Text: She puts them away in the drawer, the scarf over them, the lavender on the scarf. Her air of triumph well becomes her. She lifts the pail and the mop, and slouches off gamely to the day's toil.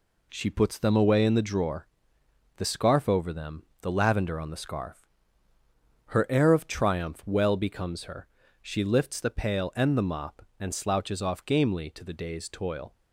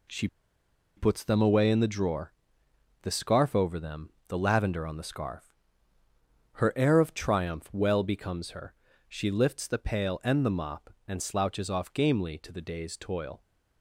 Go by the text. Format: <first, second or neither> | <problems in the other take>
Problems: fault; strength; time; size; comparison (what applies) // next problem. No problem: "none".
first | pauses between "She" and "puts"; noticeable; at 0.2 s; 0.70 s long